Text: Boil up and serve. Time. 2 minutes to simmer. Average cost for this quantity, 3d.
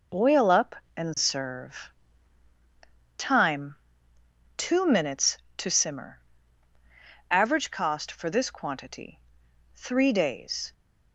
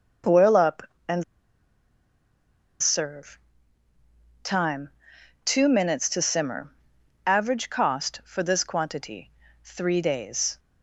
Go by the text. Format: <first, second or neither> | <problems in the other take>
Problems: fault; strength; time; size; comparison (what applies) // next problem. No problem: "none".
first | pauses between "and" and "serve"; strong; at 1.2 s; 1.6 s long